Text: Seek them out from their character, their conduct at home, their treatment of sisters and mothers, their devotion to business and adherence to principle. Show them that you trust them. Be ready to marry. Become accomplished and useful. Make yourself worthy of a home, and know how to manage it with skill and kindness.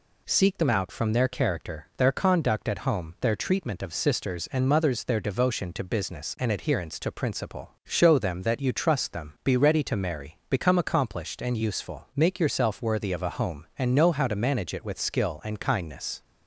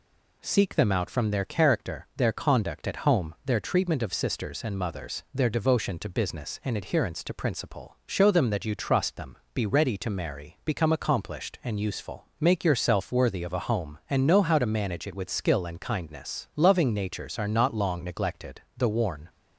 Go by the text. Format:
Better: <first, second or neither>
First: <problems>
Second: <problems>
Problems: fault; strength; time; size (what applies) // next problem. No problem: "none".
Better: first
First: none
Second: goes on to say "Loving natures are not long neglected The worn"; strong; from 16.5 s on; 2.7 s long